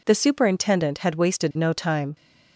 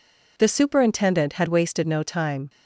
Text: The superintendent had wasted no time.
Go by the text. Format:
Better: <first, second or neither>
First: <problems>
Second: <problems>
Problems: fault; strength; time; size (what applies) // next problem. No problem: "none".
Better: neither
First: none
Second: none